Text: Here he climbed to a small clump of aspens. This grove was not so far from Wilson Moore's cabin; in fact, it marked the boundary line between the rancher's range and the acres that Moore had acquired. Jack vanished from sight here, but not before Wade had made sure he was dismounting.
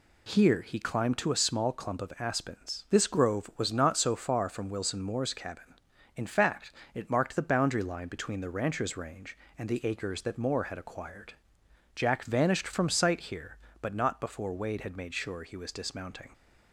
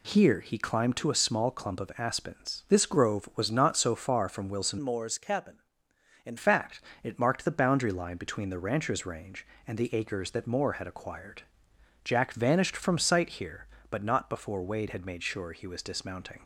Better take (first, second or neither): first